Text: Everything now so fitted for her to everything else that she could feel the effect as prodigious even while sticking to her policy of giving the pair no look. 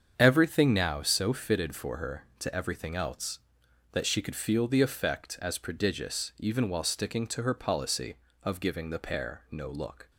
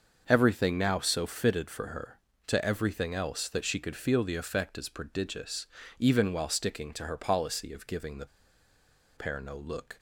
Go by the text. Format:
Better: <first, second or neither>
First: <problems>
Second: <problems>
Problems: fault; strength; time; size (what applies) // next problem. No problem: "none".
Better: first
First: starts louder than the rest; strong; until 1.1 s; 7.5 dB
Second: starts louder than the rest; until 1.2 s; 6.5 dB // pauses between "prodigious" and "even"; slight; at 5.6 s; 0.32 s long // pauses between "the" and "pair"; noticeable; at 8.2 s; 0.89 s long